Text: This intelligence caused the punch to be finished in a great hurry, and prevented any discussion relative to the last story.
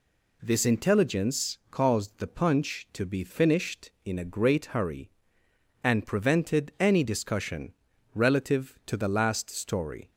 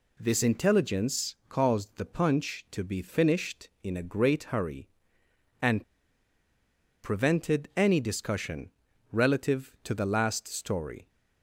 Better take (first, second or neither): first